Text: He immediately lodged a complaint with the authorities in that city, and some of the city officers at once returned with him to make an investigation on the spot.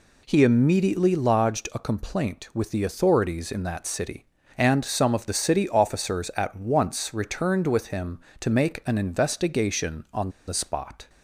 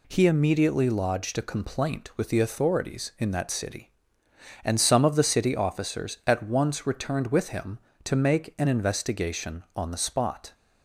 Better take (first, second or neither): second